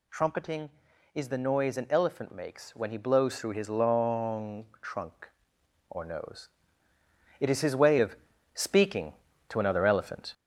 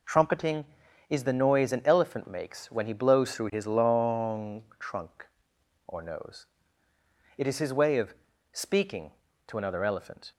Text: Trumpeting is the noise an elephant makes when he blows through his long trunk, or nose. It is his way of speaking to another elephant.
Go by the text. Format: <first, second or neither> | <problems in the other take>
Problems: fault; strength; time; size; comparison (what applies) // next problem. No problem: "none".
second | gets louder; throughout; 3.5 dB // pauses between "long" and "trunk"; slight; at 4.6 s; 0.18 s long; slight in the second // pauses between "of" and "speaking"; at 8.1 s; 0.40 s long; also in the second